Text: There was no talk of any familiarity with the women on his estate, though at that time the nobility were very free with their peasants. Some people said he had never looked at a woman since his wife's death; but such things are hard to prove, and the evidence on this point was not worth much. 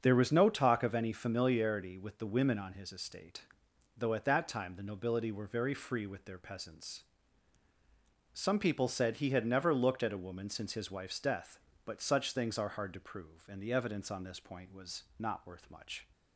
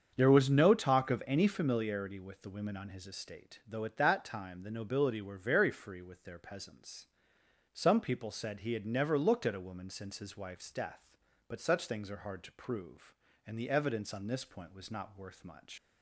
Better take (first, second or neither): first